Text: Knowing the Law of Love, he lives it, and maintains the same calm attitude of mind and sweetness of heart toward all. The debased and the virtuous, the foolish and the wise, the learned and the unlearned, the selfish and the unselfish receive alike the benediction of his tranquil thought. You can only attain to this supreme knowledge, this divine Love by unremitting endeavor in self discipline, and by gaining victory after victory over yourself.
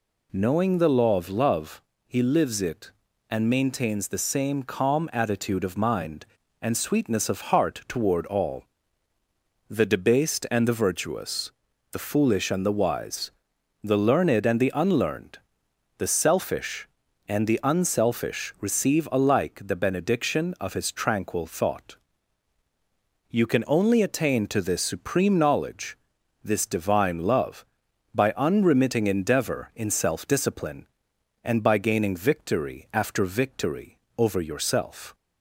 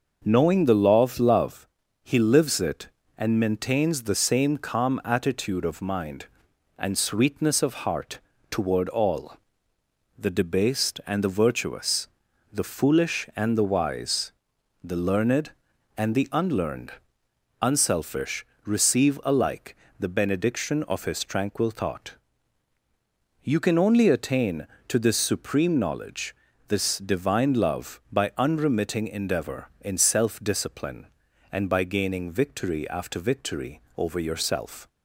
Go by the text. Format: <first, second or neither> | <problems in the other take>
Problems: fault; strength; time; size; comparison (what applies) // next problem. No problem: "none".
first | pauses between "heart" and "toward"; slight; at 8.1 s; 0.30 s long // skips "the selfish and the"; at 17.2 s // pauses between "unselfish" and "receive"; slight; at 18.4 s; 0.18 s long // pauses between "alike" and "the"; slight; at 19.7 s; 0.22 s long // pauses between "victory" and "over"; slight; at 33.8 s; 0.16 s long; slight in the first